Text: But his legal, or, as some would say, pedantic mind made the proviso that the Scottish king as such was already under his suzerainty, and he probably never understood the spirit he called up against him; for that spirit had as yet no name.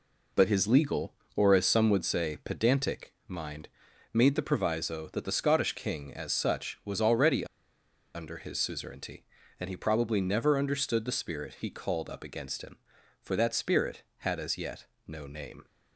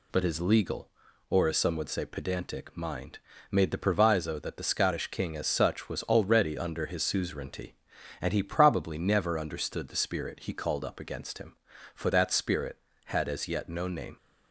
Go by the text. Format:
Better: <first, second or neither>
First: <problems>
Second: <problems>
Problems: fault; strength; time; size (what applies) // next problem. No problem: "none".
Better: second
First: pauses between "mind" and "made"; at 3.6 s; 0.44 s long // pauses between "already" and "under"; noticeable; at 7.4 s; 0.69 s long // pauses between "yet" and "no"; slight; at 14.8 s; 0.22 s long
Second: pauses between "mind" and "made"; slight; at 3.1 s; 0.34 s long